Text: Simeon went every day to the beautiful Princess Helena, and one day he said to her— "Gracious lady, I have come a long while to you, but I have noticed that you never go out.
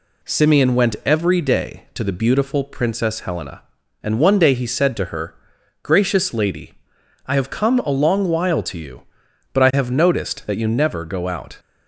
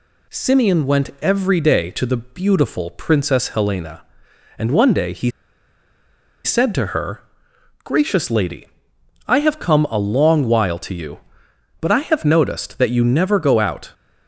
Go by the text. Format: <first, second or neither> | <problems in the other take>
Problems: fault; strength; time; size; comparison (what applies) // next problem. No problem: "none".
first | pauses between "he" and "said"; at 5.3 s; 1.1 s long